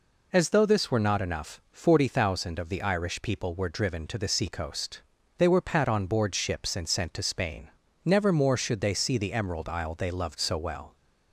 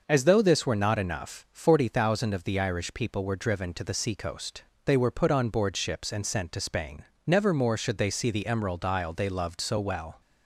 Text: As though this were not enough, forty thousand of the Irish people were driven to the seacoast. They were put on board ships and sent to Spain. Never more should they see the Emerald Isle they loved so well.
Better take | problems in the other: second | says "pat" for "put"; at 5.6 s

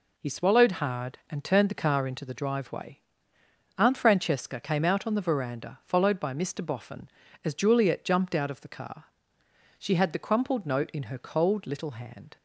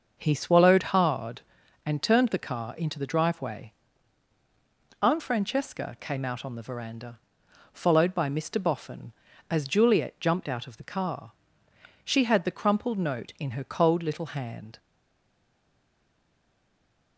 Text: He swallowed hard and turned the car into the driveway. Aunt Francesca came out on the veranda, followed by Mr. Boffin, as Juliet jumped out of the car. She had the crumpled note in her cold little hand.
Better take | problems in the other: first | starts louder than the rest; until 1.3 s; 6 dB // stays silent after the last word; from 14.7 s on; 2.4 s long

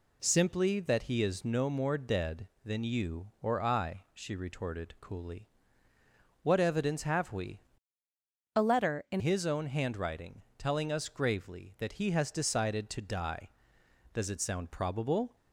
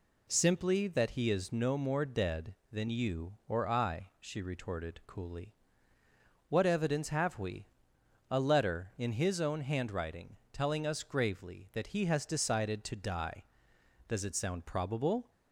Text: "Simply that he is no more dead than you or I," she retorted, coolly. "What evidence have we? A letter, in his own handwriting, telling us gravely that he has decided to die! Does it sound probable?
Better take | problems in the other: second | changes voice from "A" to "in"; from 8.5 to 9.1 s; 0.6 s long

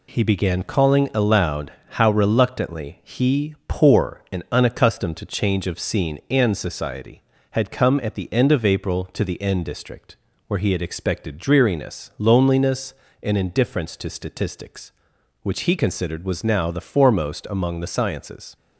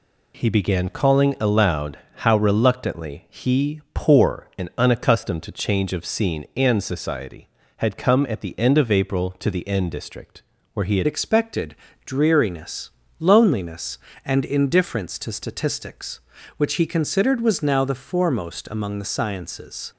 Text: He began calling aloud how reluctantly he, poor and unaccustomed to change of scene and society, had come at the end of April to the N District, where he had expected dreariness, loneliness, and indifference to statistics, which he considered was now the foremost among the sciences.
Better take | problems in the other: first | pauses between "aloud" and "how"; slight; at 1.9 s; 0.18 s long; slight in the first // changes voice at "expected"; from 11.0 s on; 8.9 s long // pauses between "expected" and "dreariness"; slight; at 11.7 s; 0.30 s long

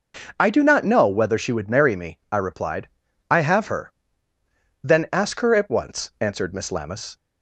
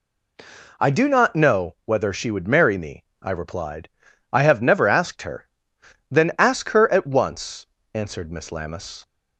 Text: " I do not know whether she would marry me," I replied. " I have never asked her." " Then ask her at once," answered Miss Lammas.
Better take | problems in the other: second | starts louder than the rest; noticeable; until 1.2 s; 6 dB // skips "never asked"; at 3.6 s

